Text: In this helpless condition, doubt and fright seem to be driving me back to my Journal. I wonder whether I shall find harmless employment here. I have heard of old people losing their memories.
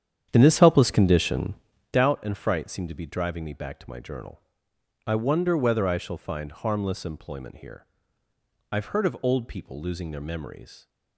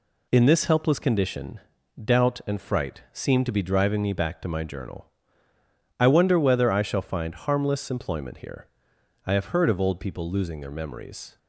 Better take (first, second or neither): second